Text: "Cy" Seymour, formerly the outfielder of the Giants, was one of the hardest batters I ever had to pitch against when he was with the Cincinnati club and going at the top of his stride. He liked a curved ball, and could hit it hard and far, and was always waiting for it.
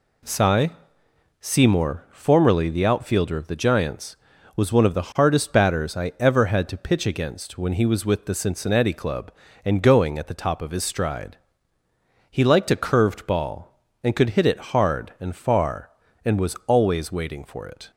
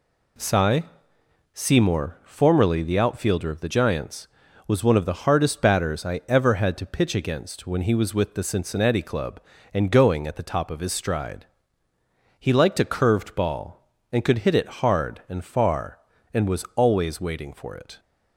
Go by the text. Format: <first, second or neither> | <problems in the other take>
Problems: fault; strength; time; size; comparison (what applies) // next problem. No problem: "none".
neither | pauses between "Cy" and "Seymour"; noticeable; the same in both